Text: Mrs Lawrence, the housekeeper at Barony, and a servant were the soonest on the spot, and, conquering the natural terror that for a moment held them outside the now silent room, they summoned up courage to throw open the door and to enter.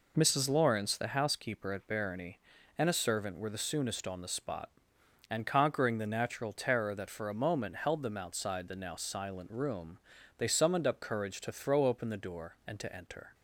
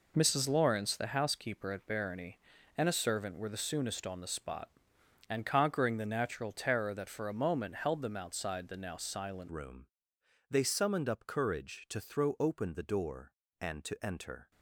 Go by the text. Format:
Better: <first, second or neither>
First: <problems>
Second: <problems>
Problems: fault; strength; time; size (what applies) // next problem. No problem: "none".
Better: first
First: none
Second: changes voice at "room"; from 9.4 s on; 5.1 s long